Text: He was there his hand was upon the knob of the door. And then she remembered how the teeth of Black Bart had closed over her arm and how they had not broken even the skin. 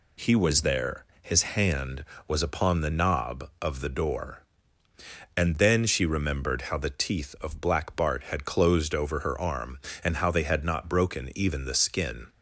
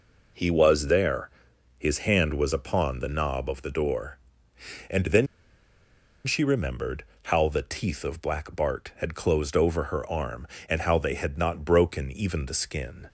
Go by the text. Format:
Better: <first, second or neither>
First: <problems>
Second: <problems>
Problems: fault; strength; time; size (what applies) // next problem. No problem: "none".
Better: first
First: pauses between "there" and "his"; slight; at 1.0 s; 0.18 s long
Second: pauses between "there" and "his"; noticeable; at 1.3 s; 0.48 s long // pauses between "then" and "she"; at 5.2 s; 1.0 s long // pauses between "remembered" and "how"; slight; at 7.0 s; 0.22 s long